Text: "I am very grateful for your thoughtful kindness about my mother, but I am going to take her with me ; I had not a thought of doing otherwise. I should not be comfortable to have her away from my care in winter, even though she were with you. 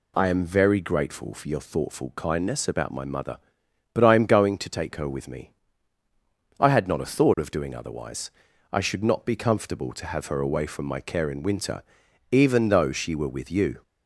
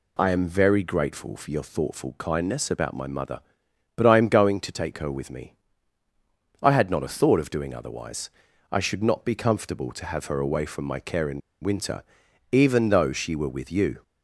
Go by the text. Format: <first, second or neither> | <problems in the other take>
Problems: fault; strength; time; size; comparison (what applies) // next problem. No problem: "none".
first | pauses between "in" and "winter"; slight; at 11.4 s; 0.24 s long